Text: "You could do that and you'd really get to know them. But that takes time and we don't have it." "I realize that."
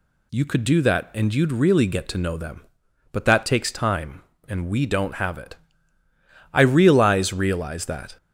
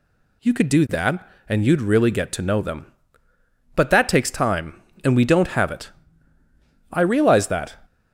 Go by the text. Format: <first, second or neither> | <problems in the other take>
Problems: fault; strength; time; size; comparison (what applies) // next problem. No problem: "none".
second | says "realize" twice; at 7.3 s